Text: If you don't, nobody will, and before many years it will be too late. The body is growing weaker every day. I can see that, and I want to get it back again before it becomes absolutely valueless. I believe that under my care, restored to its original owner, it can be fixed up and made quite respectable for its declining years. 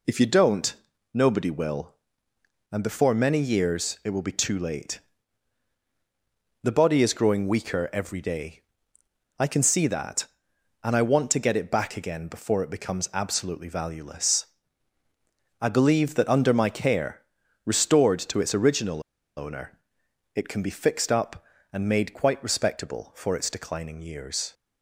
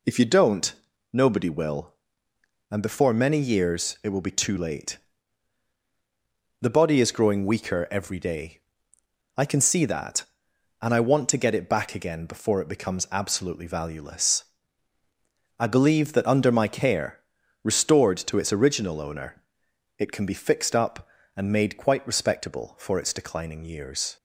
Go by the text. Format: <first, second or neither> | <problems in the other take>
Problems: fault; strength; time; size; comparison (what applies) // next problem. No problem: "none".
second | pauses between "original" and "owner"; slight; at 19.0 s; 0.36 s long